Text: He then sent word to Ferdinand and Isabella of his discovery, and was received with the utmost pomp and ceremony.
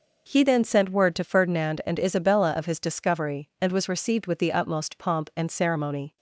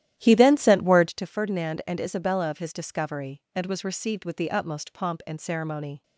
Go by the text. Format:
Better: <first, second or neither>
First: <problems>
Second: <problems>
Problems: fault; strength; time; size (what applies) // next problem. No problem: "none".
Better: first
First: none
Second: starts louder than the rest; strong; until 1.1 s; 12.5 dB